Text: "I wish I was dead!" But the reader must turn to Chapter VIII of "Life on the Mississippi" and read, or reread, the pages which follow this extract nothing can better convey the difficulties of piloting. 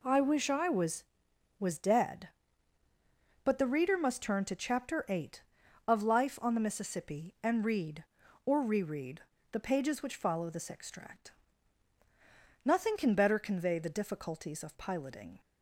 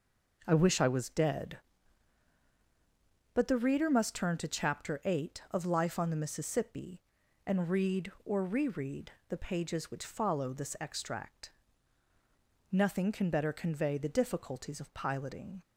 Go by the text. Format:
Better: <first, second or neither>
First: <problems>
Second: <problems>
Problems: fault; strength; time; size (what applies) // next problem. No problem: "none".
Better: second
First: says "was" twice; at 1.6 s // pauses between "extract" and "nothing"; strong; at 11.3 s; 1.3 s long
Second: pauses between "extract" and "nothing"; at 11.5 s; 1.2 s long